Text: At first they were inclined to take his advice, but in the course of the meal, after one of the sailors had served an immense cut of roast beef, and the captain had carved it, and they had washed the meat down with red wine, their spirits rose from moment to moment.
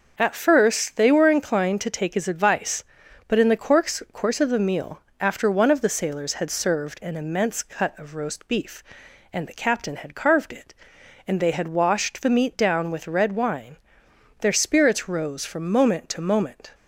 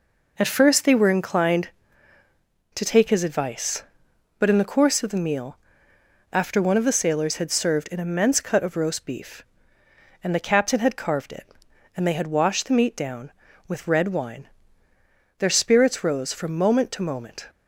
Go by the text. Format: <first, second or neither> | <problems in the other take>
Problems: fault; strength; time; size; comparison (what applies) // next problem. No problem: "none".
second | says "course" twice; at 4.1 s